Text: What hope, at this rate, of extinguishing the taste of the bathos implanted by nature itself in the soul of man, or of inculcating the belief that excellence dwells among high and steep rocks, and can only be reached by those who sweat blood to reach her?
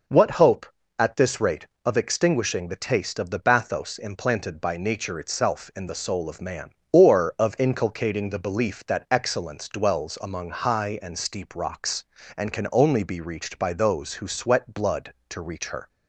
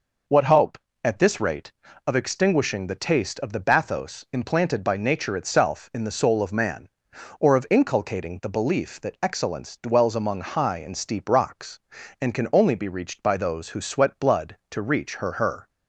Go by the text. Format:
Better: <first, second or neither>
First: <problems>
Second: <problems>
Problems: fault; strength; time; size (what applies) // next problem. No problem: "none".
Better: first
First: none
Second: says "her" twice; at 15.3 s